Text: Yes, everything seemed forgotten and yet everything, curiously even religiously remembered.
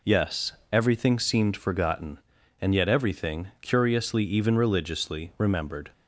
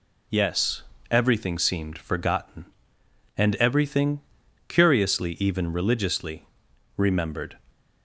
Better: first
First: none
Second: skips "yet"; at 3.5 s // pauses between "religiously" and "remembered"; noticeable; at 6.4 s; 0.50 s long

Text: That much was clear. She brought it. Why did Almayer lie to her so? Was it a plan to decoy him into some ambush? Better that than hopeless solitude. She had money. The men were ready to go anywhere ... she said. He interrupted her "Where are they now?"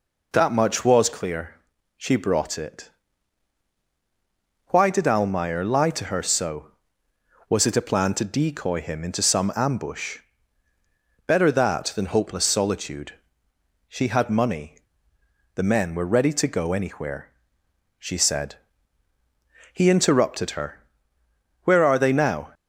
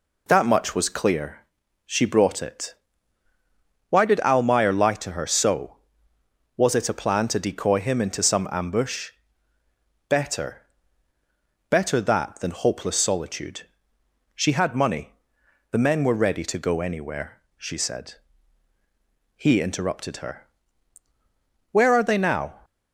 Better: first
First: pauses between "her" and "Where"; noticeable; at 20.7 s; 0.84 s long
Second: says "Better" twice; at 11.6 s // pauses between "her" and "Where"; at 20.4 s; 1.2 s long

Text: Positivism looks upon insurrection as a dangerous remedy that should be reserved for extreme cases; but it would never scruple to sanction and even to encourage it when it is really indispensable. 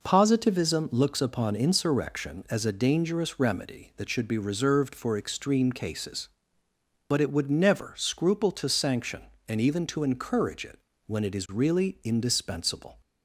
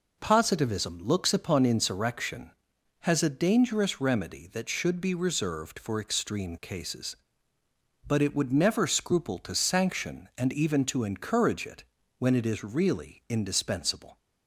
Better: first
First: pauses between "it" and "when"; slight; at 10.7 s; 0.28 s long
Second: says "has" for "as"; at 3.0 s // pauses between "it" and "when"; slight; at 11.8 s; 0.36 s long

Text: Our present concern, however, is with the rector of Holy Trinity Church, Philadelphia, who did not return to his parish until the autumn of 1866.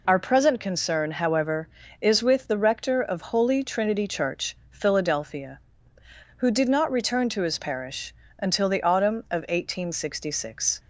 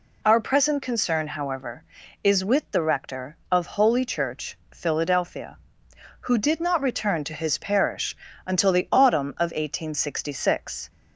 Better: first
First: pauses between "parish" and "until"; slight; at 8.1 s; 0.24 s long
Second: skips "Trinity"; at 4.0 s // pauses between "parish" and "until"; slight; at 8.1 s; 0.30 s long

